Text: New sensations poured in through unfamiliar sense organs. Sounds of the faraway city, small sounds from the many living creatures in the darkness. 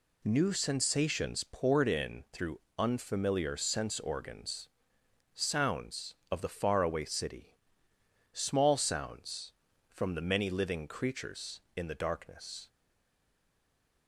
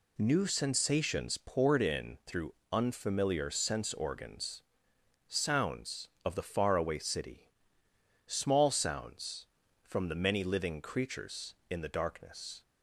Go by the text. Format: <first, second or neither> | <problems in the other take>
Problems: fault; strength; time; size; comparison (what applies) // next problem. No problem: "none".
second | pauses between "through" and "unfamiliar"; slight; at 2.6 s; 0.18 s long; slight in the second // stays silent after the last word; noticeable; from 12.6 s on; 1.4 s long